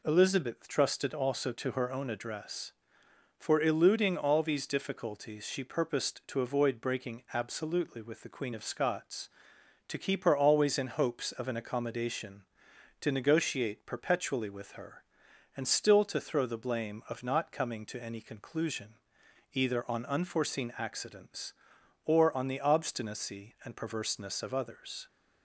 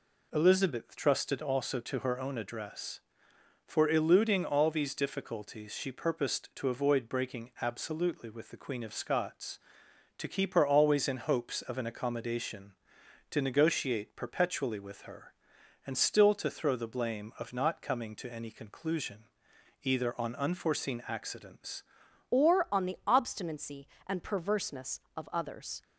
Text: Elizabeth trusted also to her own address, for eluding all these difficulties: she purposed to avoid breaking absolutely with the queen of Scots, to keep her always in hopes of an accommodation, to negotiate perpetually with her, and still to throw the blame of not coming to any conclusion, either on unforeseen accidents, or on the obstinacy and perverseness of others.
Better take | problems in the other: first | changes voice at "or"; from 22.3 s on; 3.5 s long

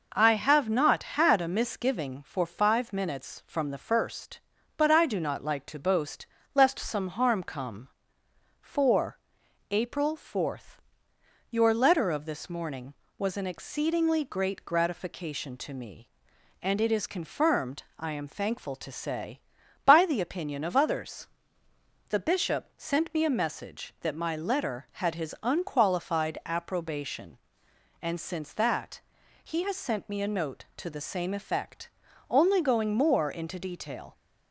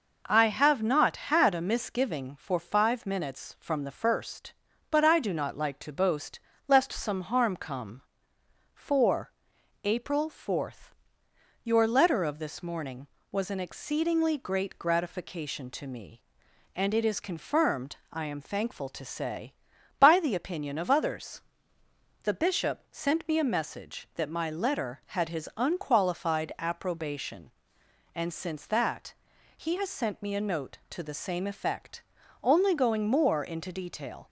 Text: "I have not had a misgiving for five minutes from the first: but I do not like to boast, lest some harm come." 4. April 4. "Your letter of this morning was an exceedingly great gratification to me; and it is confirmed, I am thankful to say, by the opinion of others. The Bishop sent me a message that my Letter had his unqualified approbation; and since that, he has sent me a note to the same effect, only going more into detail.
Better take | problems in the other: neither | none

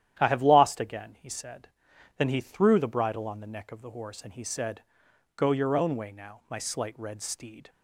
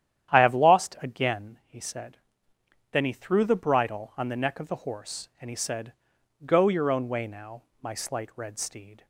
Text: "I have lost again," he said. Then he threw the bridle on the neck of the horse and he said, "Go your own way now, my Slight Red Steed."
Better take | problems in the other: neither | starts louder than the rest; strong; the same in both

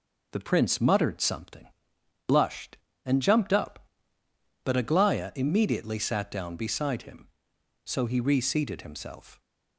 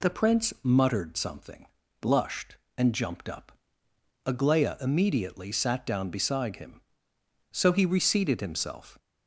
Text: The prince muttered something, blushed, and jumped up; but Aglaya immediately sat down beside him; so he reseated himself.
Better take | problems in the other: first | skips "but"; at 3.8 s

